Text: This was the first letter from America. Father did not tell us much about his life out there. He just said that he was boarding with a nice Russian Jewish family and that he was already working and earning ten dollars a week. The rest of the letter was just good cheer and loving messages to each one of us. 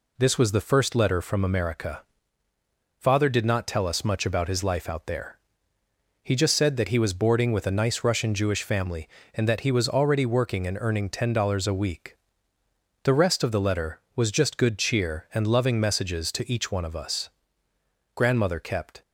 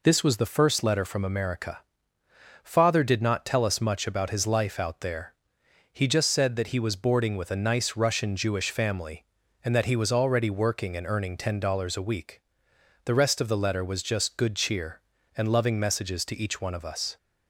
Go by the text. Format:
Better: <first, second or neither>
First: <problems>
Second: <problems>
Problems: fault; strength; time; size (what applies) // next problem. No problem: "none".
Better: second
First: goes on to say "Grandmother kept"; noticeable; from 18.1 s on; 0.86 s long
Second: none